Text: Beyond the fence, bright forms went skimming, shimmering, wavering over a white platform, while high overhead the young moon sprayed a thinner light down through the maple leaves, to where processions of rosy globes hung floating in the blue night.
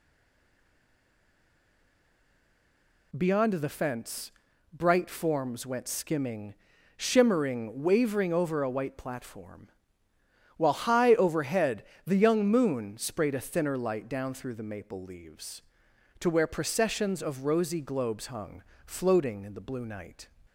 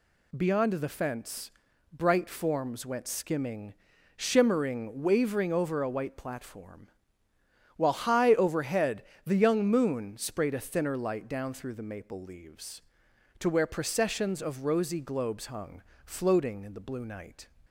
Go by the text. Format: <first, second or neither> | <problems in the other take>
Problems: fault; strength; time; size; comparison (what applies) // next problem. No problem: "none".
second | stays silent before the first word; strong; until 3.1 s; 3.1 s long // pauses between "overhead" and "the"; slight; at 11.8 s; 0.24 s long; slight in the second // pauses between "hung" and "floating"; slight; at 18.6 s; 0.24 s long; slight in the second